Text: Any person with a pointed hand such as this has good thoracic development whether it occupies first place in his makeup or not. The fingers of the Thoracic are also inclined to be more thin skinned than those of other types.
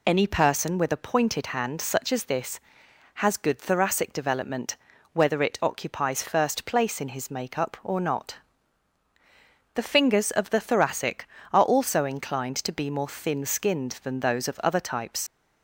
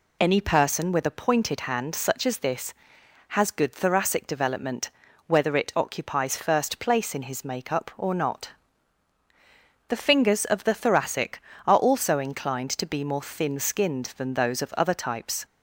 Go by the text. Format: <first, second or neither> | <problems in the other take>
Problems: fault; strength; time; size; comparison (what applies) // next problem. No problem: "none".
second | pauses between "development" and "whether"; slight; at 4.7 s; 0.36 s long; slight in the second // leaves "types" unfinished; at 15.2 s; 40 ms